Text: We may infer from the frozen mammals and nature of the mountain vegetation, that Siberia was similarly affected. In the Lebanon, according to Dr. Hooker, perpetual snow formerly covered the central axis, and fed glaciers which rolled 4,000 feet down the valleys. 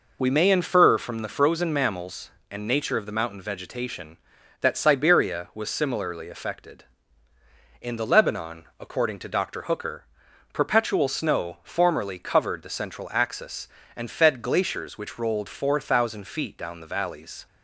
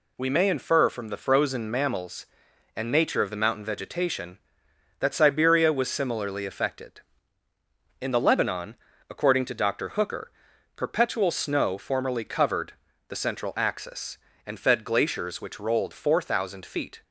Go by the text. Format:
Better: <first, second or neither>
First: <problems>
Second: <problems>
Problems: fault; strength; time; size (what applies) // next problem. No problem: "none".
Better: first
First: none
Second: pauses between "covered" and "the"; slight; at 12.7 s; 0.36 s long // stops before "down the valleys"; at 17.0 s